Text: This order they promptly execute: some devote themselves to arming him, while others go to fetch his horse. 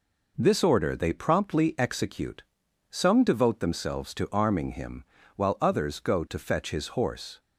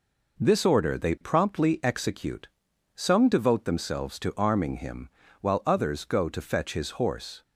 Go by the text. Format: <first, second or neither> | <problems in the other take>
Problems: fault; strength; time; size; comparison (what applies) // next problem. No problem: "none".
neither | none